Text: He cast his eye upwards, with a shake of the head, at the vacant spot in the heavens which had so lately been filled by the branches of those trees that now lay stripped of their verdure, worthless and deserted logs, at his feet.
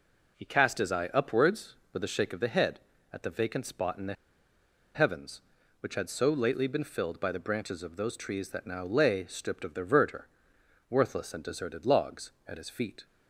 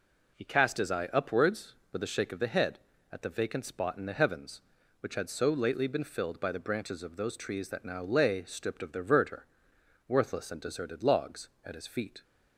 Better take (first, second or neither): second